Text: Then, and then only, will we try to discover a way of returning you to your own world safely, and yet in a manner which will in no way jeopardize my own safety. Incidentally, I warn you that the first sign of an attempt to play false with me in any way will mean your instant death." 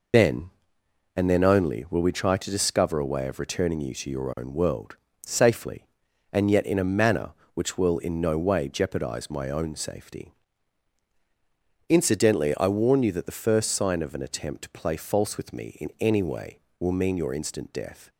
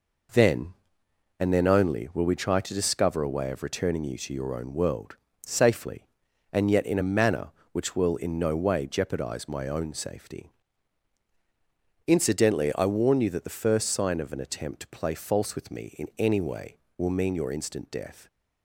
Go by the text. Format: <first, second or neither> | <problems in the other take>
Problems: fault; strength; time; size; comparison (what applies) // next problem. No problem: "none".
second | loses the start of "Then"; at 0.1 s; 65 ms // pauses between "world" and "safely"; slight; at 4.9 s; 0.30 s long; slight in the second